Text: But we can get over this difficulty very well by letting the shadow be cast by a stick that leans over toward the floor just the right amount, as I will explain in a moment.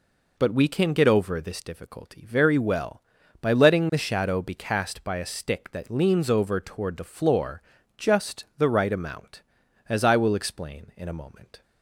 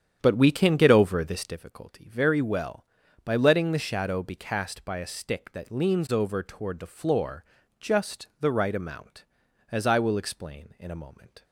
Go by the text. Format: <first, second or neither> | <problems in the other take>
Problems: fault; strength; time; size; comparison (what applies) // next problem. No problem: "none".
first | starts louder than the rest; strong; until 1.6 s; 9 dB // pauses between "floor" and "just"; slight; at 7.4 s; 0.36 s long; slight in the first